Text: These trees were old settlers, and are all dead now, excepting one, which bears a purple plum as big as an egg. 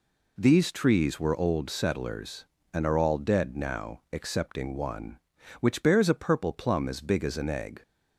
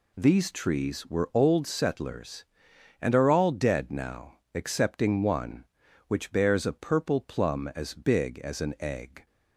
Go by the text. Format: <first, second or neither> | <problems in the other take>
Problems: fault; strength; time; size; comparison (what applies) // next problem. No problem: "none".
neither | none